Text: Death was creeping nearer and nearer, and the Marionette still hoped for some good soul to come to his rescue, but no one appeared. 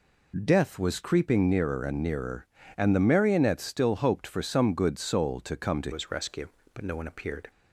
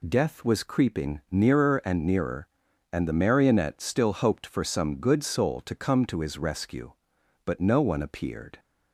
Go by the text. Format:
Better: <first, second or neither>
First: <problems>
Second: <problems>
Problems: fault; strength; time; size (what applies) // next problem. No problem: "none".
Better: second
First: changes voice at "his"; from 5.9 s on; 1.6 s long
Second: none